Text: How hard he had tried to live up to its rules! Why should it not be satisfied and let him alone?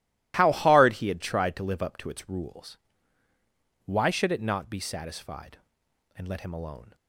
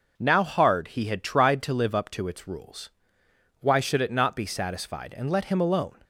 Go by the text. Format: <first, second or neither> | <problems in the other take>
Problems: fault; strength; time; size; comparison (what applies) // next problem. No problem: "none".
first | says "Now" for "How"; at 0.1 s